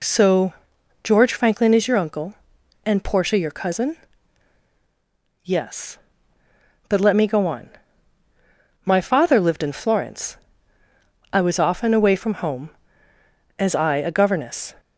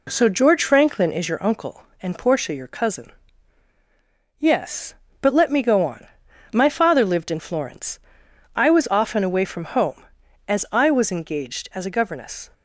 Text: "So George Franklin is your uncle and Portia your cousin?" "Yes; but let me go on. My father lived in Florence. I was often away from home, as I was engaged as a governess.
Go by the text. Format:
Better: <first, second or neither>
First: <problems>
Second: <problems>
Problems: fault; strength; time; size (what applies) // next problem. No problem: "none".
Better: second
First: pauses between "So" and "George"; noticeable; at 0.5 s; 0.52 s long // skips "was engaged as"; at 13.9 s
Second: none